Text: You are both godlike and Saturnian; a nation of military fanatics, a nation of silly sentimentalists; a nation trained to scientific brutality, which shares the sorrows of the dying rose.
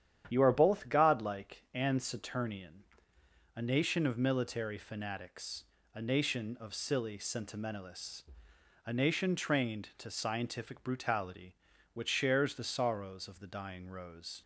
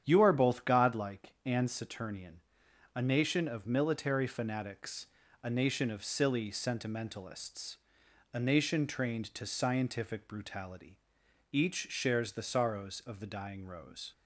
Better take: first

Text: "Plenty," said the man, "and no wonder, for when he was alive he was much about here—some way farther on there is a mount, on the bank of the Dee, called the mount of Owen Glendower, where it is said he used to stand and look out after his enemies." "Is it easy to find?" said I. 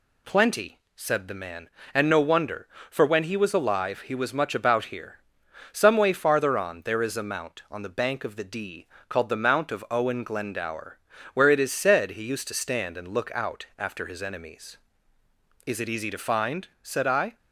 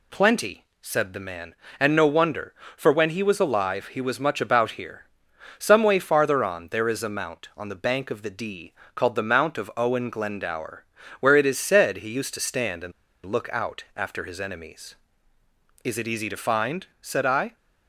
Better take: first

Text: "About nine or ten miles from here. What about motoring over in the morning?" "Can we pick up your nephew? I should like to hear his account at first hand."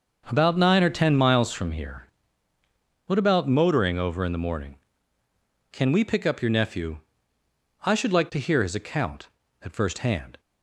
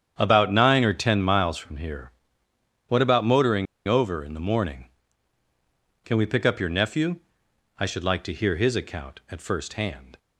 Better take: first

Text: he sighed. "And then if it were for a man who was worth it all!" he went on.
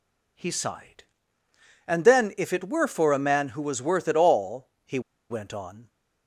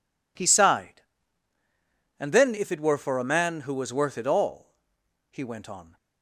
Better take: second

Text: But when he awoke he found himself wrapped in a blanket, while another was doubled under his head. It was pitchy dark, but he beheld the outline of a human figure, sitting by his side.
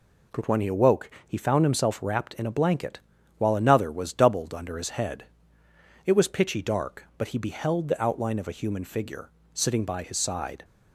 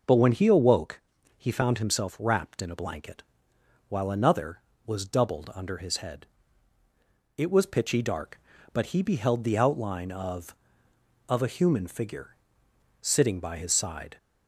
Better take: first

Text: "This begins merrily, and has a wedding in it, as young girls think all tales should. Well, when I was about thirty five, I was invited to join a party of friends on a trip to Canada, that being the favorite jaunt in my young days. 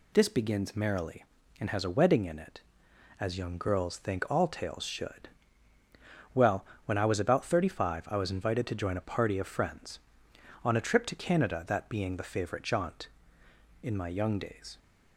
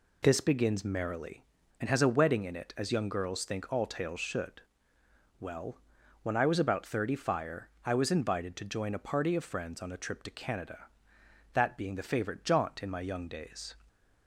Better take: first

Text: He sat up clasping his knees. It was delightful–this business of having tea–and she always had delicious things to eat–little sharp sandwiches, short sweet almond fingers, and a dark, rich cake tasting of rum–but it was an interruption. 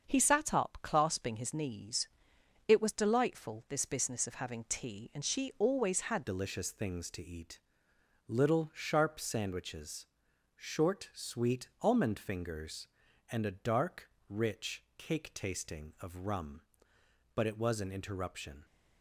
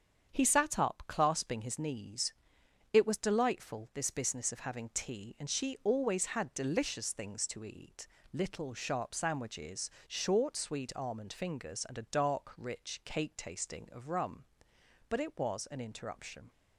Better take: second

